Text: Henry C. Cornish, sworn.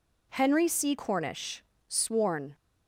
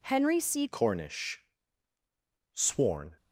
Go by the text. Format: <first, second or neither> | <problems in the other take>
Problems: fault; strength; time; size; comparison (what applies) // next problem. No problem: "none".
first | changes voice at "Cornish"; from 0.6 s on; 2.5 s long